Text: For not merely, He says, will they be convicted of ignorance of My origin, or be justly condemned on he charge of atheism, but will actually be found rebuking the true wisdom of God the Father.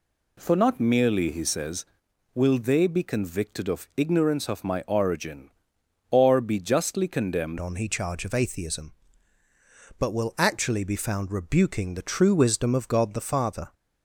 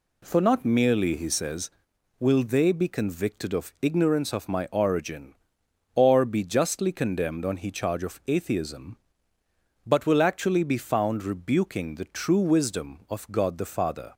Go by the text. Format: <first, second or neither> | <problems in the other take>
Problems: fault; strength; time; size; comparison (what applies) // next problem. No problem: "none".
second | changes voice at "on"; from 7.5 s on; 6.2 s long